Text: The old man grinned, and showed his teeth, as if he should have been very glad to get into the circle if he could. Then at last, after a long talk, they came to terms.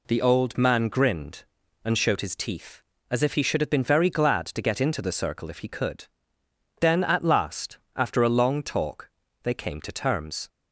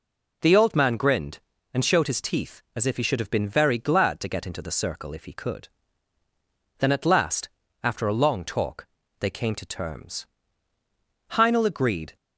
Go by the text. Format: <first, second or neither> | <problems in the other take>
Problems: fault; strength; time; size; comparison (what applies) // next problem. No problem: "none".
first | goes on to say "Heinel agreed"; noticeable; from 11.3 s on; 0.84 s long